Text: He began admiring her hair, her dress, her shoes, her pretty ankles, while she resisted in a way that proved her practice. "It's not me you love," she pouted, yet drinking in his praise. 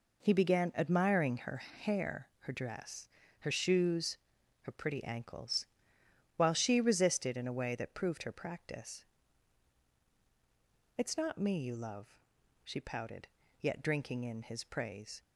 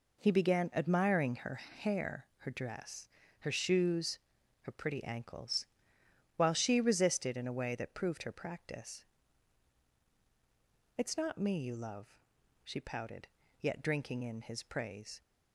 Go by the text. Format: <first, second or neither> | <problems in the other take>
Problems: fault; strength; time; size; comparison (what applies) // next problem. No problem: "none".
neither | none